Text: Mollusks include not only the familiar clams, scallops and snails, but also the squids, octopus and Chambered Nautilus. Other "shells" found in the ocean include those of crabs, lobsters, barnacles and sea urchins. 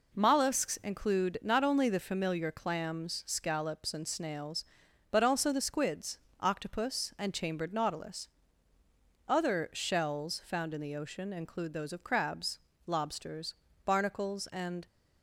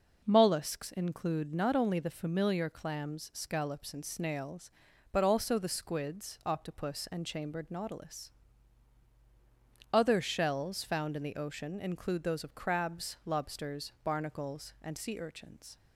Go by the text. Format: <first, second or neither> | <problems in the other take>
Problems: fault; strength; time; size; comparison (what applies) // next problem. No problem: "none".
second | stops before "sea urchins"; at 14.8 s